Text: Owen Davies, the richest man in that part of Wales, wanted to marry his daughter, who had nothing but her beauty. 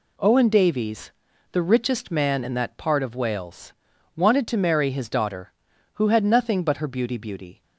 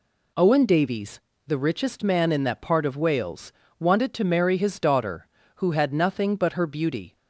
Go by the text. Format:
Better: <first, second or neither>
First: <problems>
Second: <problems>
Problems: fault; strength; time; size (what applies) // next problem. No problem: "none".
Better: second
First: says "beauty" twice; at 7.1 s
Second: none